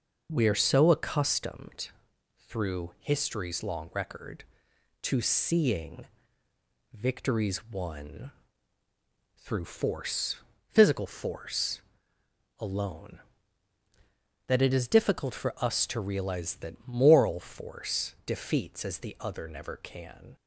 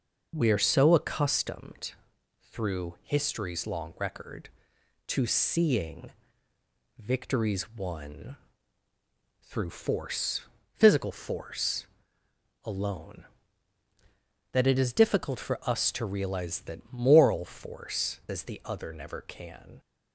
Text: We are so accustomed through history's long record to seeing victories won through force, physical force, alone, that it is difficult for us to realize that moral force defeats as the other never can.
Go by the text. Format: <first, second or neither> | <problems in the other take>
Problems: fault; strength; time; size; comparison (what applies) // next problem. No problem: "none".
first | pauses between "accustomed" and "through"; noticeable; at 1.9 s; 0.58 s long; noticeable in the first // pauses between "seeing" and "victories"; noticeable; at 6.1 s; 0.88 s long; noticeable in the first // pauses between "won" and "through"; at 8.3 s; 1.0 s long; also in the first // skips "defeats"; at 18.2 s